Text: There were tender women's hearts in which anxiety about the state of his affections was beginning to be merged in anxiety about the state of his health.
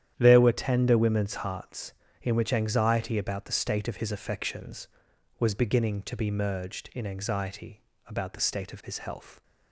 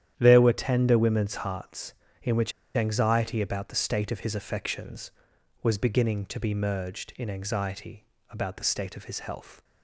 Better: first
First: starts louder than the rest; strong; until 1.1 s; 10 dB // pauses between "anxiety" and "about"; slight; at 7.8 s; 0.26 s long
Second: starts louder than the rest; strong; until 1.1 s; 10 dB // pauses between "which" and "anxiety"; slight; at 2.5 s; 0.23 s long // pauses between "anxiety" and "about"; slight; at 8.0 s; 0.26 s long

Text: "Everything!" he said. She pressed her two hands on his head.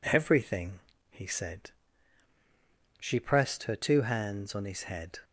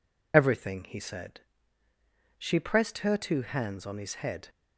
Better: first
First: none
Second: loses the start of "Everything"; at 0.3 s; 50 ms

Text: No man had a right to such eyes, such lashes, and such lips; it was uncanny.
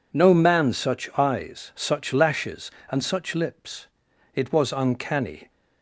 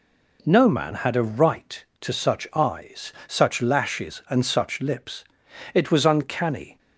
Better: second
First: skips "had a right to"; at 0.7 s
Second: none

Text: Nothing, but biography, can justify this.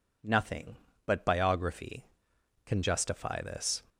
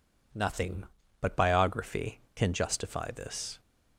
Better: neither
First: none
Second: none

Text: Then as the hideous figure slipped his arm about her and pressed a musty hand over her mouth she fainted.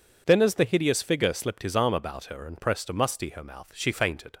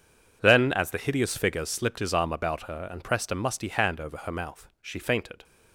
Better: second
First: skips "hand over"; at 3.2 s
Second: none

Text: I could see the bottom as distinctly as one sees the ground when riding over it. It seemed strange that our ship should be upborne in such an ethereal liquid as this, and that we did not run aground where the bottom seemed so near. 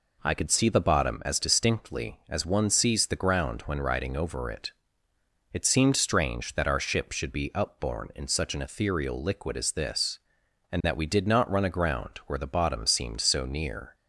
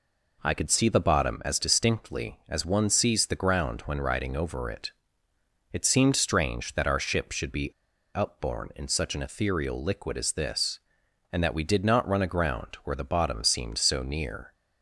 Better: first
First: none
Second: pauses between "be" and "upborne"; at 7.7 s; 0.41 s long

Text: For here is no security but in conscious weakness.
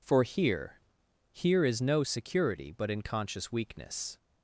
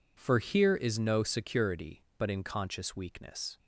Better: second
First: says "here" twice; at 1.3 s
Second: none

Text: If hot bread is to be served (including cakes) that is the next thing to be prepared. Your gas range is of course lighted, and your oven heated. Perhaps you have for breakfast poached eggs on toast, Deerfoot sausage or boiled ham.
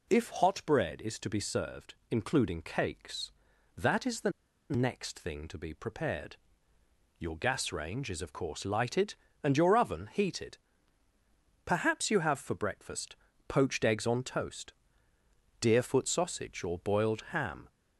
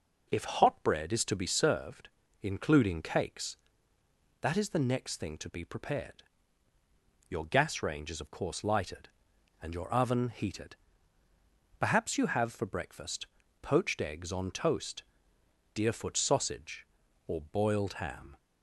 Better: second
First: pauses between "the" and "next"; at 4.2 s; 0.40 s long // pauses between "breakfast" and "poached"; slight; at 13.1 s; 0.32 s long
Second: pauses between "breakfast" and "poached"; at 13.2 s; 0.38 s long

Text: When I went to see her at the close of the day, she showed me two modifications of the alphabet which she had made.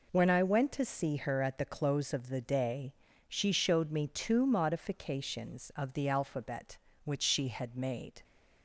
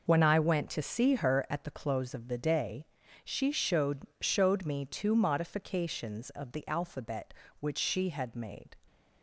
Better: first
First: none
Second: says "showed" twice; at 4.2 s

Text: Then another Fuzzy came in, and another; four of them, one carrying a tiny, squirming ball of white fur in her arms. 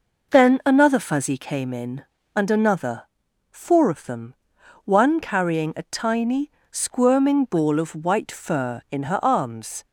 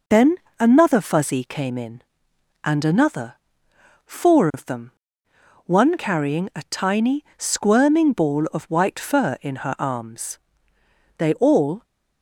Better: first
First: none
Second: pauses between "Then" and "another"; slight; at 0.3 s; 0.24 s long // goes on to say "They all"; noticeable; from 11.1 s on; 0.64 s long

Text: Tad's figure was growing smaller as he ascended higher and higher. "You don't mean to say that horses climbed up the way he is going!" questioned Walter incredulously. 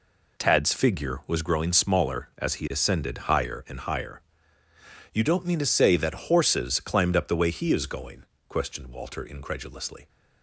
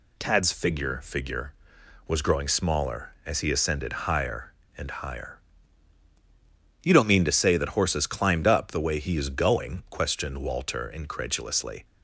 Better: first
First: none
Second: says "figure" twice; at 1.0 s

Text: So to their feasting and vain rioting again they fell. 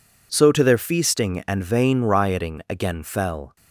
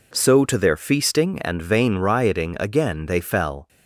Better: second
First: skips "they"; at 3.0 s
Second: none

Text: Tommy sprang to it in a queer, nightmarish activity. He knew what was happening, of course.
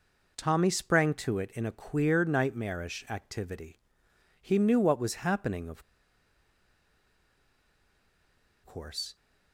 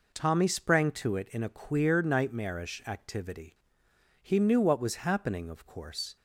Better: second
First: pauses between "of" and "course"; strong; at 5.8 s; 2.8 s long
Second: none

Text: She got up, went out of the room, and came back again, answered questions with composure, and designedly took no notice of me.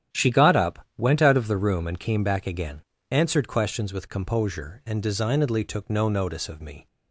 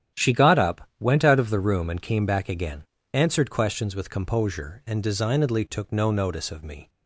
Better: neither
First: starts louder than the rest; strong; until 1.2 s; 9 dB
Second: starts louder than the rest; strong; until 1.2 s; 9 dB

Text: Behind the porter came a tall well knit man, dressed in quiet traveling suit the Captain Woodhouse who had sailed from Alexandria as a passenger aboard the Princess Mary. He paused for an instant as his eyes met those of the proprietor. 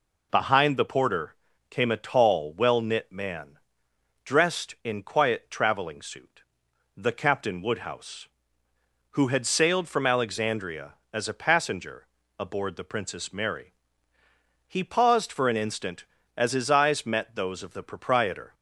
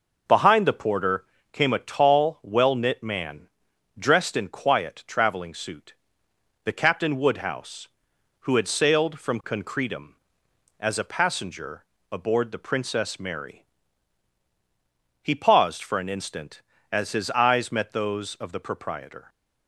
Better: first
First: pauses between "porter" and "came"; slight; at 1.3 s; 0.36 s long // pauses between "suit" and "the"; noticeable; at 6.4 s; 0.52 s long // pauses between "passenger" and "aboard"; slight; at 12.0 s; 0.32 s long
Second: pauses between "porter" and "came"; slight; at 1.2 s; 0.28 s long // pauses between "suit" and "the"; noticeable; at 5.9 s; 0.70 s long // says "Concretum" for "Alexandria"; at 9.4 s // pauses between "passenger" and "aboard"; slight; at 11.8 s; 0.26 s long

